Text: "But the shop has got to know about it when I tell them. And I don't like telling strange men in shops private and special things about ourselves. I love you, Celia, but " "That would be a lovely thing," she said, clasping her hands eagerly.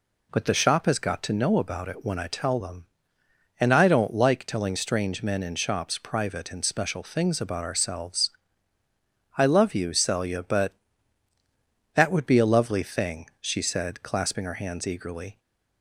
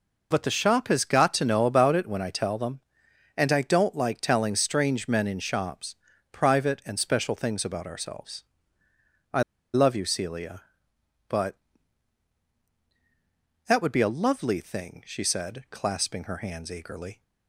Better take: first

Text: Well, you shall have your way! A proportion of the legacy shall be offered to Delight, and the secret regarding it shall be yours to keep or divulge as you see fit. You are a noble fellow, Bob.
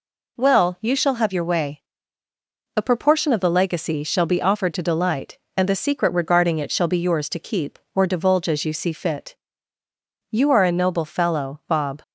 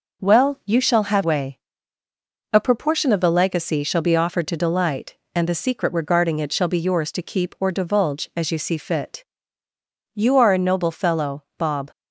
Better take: first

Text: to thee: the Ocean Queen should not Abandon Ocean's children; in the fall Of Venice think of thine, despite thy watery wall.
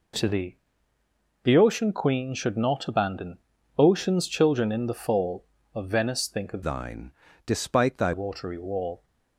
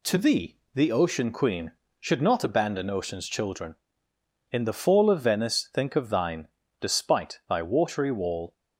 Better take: second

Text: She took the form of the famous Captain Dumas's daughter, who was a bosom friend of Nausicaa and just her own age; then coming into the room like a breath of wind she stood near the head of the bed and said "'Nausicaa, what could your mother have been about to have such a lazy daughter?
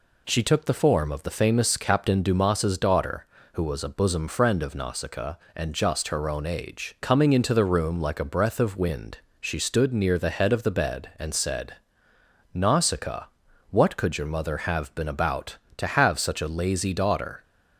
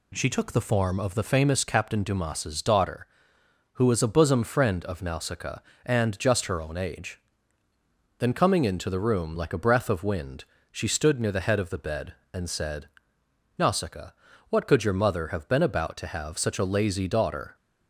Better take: second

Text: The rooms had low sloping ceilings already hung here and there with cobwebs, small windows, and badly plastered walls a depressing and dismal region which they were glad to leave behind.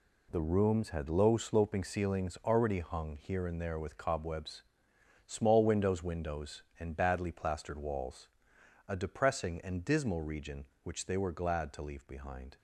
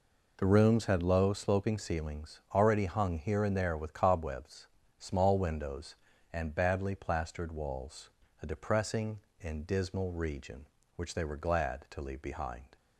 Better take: second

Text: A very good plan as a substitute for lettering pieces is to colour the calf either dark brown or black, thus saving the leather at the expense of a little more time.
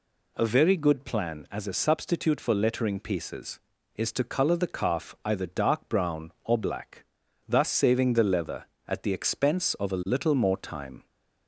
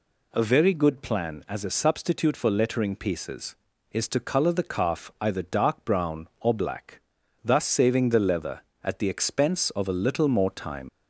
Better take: first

